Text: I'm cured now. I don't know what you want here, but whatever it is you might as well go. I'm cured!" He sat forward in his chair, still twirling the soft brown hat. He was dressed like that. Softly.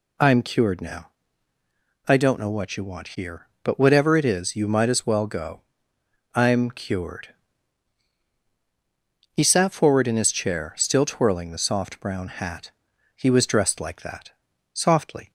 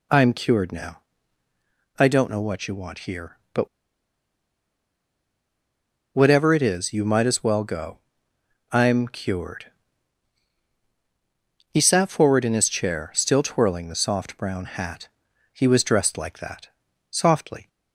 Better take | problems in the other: first | pauses between "but" and "whatever"; strong; at 3.6 s; 2.4 s long

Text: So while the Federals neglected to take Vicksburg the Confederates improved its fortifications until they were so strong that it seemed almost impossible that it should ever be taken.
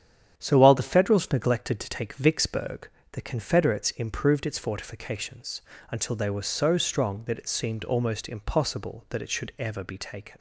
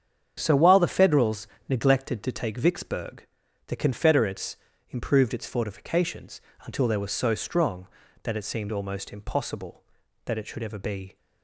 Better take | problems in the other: first | starts louder than the rest; strong; until 1.3 s; 8 dB; strong in the first // pauses between "Federals" and "neglected"; slight; at 1.4 s; 0.20 s long // pauses between "Vicksburg" and "the"; at 3.2 s; 0.40 s long; slight in the first // pauses between "Confederates" and "improved"; slight; at 4.5 s; 0.36 s long // pauses between "fortifications" and "until"; slight; at 6.4 s; 0.24 s long; slight in the first // stops before "taken"; at 11.1 s

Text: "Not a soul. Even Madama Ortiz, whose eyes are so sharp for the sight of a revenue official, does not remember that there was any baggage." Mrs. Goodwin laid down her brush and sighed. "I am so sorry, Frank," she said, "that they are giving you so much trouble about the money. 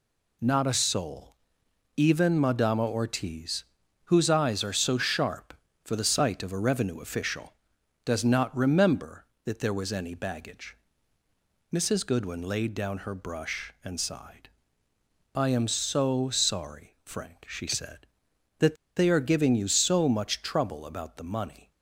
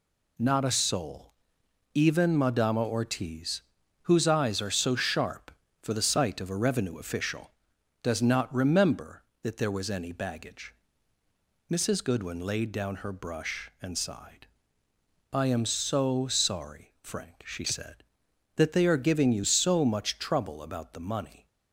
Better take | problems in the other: second | pauses between "that" and "they"; slight; at 18.7 s; 0.21 s long

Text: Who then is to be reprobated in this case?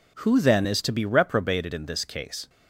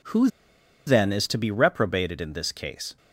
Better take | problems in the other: first | pauses between "Who" and "then"; noticeable; at 0.2 s; 0.58 s long

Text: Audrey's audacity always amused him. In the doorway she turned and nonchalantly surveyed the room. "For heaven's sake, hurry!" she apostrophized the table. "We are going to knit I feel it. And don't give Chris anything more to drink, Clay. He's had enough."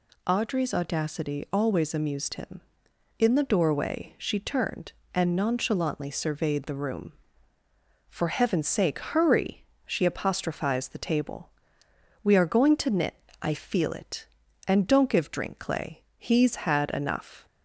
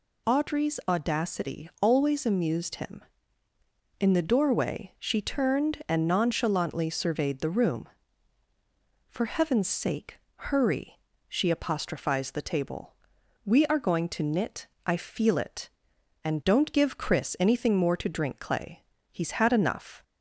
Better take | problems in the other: second | pauses between "knit" and "I"; slight; at 13.1 s; 0.24 s long; slight in the second // skips "Chris anything more to"; at 15.2 s

